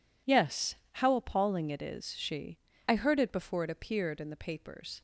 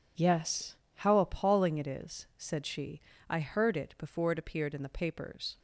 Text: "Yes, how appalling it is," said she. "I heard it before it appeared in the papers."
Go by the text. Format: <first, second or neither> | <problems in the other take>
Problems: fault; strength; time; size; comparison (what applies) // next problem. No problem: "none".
second | skips "said"; at 2.1 s